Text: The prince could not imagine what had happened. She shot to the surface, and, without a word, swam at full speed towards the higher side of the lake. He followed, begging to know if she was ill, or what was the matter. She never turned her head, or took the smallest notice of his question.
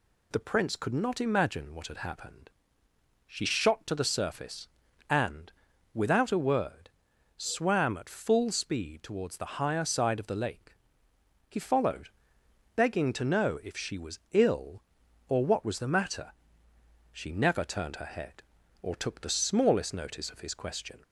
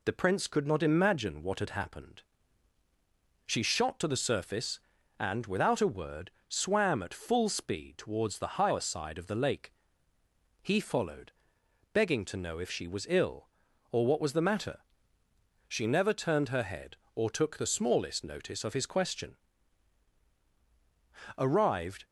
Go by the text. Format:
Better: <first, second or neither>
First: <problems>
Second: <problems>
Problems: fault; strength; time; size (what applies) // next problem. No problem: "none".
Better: first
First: none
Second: goes on to say "Arrived"; noticeable; from 21.3 s on; 0.68 s long